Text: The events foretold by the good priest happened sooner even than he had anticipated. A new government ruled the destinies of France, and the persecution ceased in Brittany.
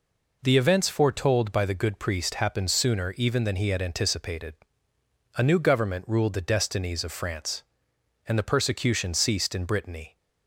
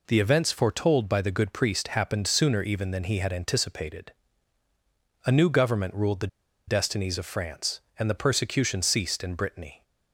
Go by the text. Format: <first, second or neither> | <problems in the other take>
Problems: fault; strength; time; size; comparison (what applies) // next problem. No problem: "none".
first | pauses between "the" and "destinies"; at 6.2 s; 0.40 s long